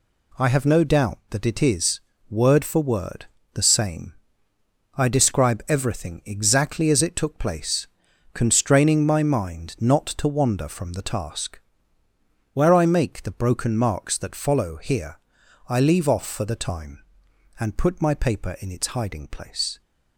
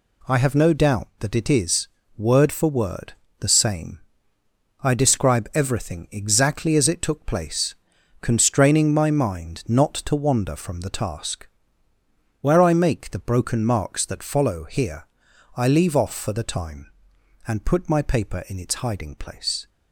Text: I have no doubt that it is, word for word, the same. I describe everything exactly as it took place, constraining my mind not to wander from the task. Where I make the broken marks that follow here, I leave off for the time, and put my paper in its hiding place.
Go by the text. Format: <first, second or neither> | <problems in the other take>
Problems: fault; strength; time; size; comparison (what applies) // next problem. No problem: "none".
neither | none